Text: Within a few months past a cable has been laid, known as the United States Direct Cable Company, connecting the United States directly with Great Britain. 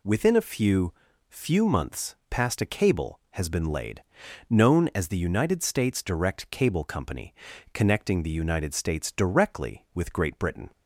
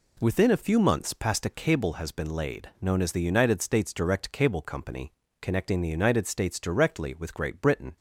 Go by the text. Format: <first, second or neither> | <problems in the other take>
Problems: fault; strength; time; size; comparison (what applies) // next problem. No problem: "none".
second | says "few" twice; at 1.2 s